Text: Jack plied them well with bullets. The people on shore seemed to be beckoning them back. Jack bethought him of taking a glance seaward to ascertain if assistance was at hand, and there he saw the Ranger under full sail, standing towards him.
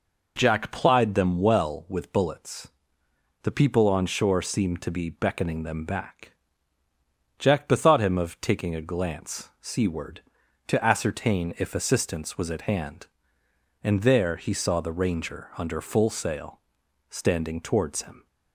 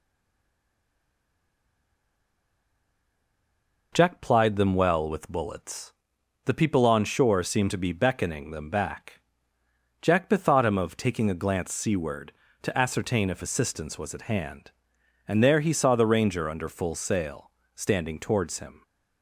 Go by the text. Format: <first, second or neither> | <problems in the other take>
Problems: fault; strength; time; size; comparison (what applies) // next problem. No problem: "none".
first | stays silent before the first word; strong; until 3.9 s; 3.9 s long